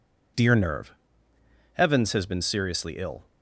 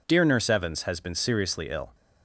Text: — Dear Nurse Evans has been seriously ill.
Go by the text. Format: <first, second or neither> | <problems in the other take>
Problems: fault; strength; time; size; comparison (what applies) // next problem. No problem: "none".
second | says "Nerve" for "Nurse"; at 0.5 s